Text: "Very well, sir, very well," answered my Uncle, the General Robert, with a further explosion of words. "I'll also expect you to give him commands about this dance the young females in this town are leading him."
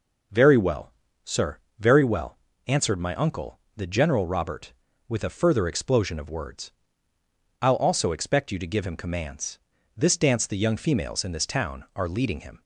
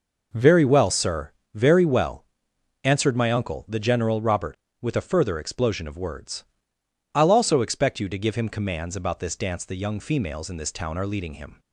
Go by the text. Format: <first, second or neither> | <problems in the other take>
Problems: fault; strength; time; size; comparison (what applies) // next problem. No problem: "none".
second | skips "about"; at 9.7 s